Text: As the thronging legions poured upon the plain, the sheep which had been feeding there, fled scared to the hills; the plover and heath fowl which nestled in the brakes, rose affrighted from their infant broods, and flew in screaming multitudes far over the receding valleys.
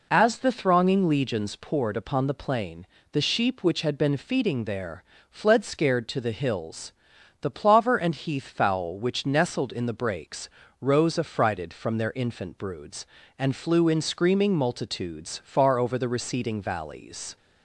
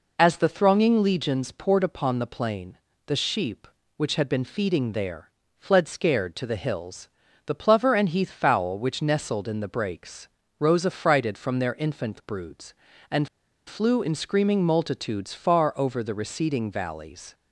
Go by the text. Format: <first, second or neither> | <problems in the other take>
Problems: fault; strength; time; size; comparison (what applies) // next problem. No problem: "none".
first | pauses between "and" and "flew"; at 13.2 s; 0.39 s long